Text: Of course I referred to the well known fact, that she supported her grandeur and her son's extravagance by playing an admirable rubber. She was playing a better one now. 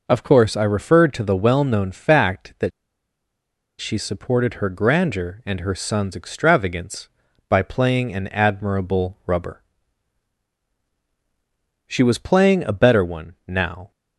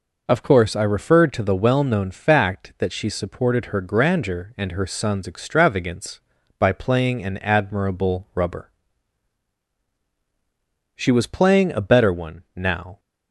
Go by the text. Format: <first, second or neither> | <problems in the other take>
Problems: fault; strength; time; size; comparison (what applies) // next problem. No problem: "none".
second | pauses between "that" and "she"; at 2.7 s; 1.1 s long